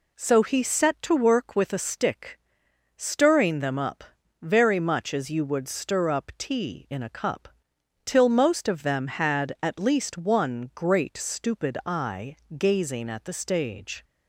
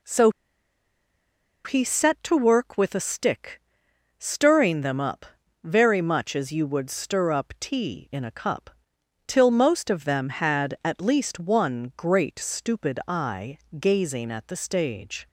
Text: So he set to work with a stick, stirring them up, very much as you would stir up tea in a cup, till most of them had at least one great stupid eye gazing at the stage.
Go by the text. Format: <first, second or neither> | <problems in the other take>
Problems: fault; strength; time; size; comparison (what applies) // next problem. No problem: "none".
first | pauses between "So" and "he"; strong; at 0.3 s; 1.3 s long // pauses between "eye" and "gazing"; slight; at 13.5 s; 0.22 s long; slight in the first